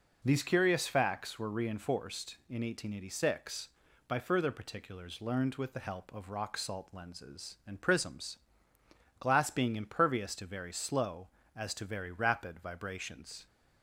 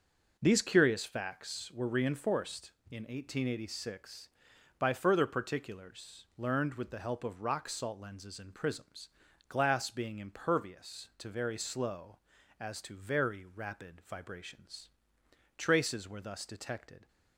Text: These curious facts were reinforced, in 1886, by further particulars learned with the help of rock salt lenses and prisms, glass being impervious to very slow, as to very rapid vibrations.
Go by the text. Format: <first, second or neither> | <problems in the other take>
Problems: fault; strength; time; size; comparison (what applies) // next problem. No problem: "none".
first | goes on to say "Traces were thus detected"; from 15.5 s on; 1.5 s long